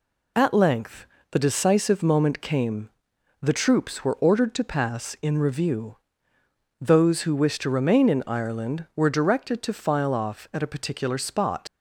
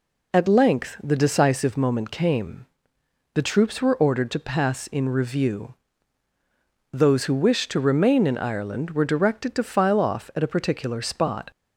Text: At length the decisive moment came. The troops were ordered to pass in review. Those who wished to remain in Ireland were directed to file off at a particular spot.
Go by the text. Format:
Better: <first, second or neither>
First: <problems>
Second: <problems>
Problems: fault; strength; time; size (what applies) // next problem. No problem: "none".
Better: second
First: pauses between "length" and "the"; slight; at 1.0 s; 0.26 s long // leaves "spot" unfinished; at 11.6 s; 105 ms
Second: none